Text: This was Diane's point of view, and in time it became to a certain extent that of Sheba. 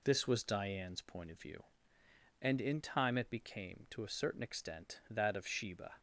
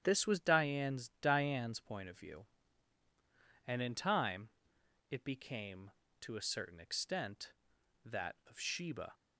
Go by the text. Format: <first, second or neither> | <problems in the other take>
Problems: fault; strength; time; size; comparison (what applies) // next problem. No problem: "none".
first | starts louder than the rest; strong; until 1.0 s; 9.5 dB // says "Diane's" twice; at 1.2 s // pauses between "time" and "it"; noticeable; at 4.4 s; 0.62 s long